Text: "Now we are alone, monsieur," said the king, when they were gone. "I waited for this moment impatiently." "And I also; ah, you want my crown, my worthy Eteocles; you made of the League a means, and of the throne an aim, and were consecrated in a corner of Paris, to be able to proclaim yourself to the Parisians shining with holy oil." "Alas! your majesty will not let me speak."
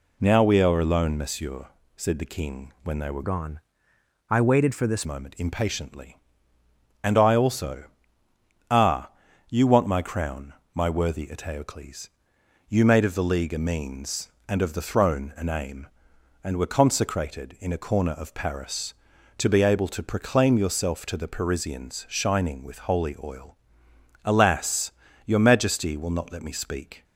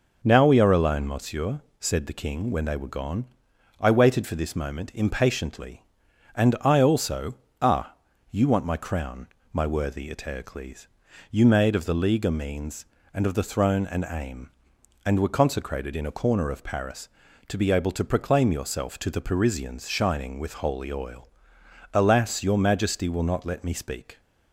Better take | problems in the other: second | changes voice from "gone" to "this"; from 3.2 to 5.0 s; 1.8 s long

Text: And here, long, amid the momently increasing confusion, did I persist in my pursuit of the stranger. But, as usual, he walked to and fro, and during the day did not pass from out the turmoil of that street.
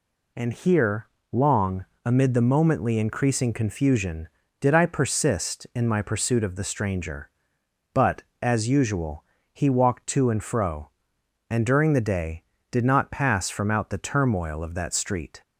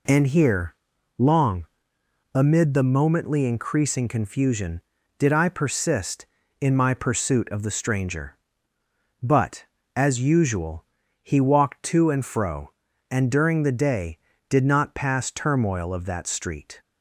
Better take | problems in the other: first | skips "from out the"; at 15.2 s

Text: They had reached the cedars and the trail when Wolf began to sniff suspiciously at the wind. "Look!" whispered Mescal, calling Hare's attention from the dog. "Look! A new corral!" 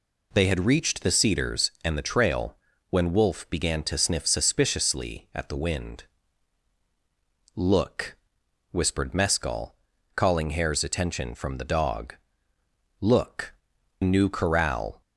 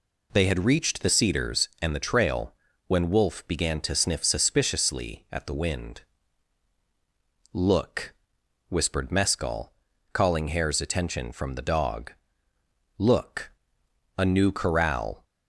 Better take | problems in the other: second | pauses between "trail" and "when"; slight; at 2.5 s; 0.34 s long; slight in the second // skips "A"; at 13.7 s

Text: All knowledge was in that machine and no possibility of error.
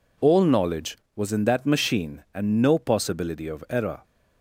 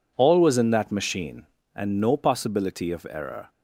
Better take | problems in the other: first | skips "knowledge"; at 0.4 s

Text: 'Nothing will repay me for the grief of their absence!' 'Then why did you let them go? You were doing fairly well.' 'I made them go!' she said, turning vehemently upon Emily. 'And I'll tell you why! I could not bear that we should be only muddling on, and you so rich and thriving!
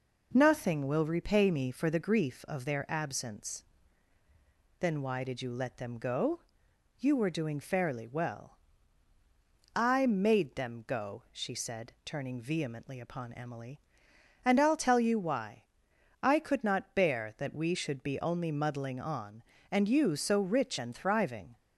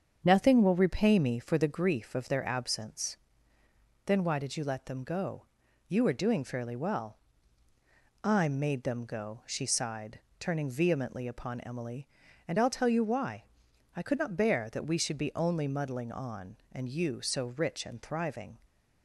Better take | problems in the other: first | starts louder than the rest; strong; until 1.2 s; 7.5 dB // says "sighed" for "said"; at 9.6 s

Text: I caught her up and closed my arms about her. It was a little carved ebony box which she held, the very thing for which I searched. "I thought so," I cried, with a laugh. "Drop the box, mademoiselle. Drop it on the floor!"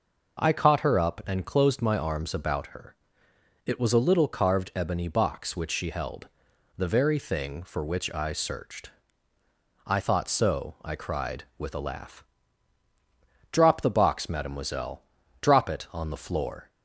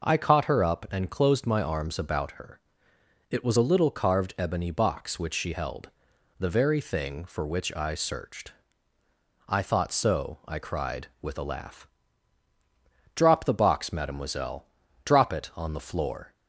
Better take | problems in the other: neither | none

